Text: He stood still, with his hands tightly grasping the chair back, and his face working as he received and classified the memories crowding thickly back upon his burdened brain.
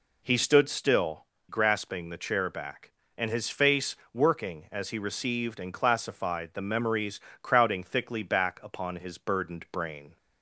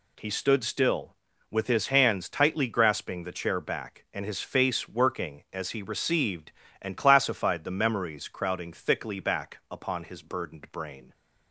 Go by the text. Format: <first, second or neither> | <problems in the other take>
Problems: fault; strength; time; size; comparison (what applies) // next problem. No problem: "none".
second | skips "with his hands tightly"; at 1.3 s // pauses between "face" and "working"; slight; at 3.9 s; 0.16 s long // pauses between "memories" and "crowding"; slight; at 7.1 s; 0.22 s long